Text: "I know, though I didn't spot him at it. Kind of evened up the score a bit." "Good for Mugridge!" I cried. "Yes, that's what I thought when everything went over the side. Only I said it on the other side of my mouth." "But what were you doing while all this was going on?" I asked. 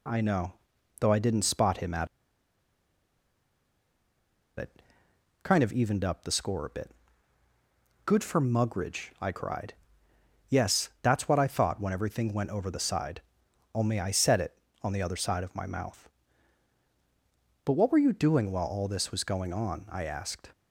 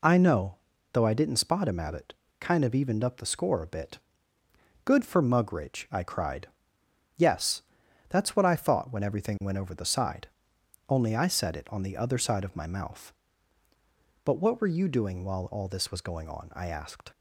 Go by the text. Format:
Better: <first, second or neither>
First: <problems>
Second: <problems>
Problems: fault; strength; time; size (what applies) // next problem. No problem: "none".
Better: second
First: pauses between "at" and "it"; strong; at 2.0 s; 2.5 s long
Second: none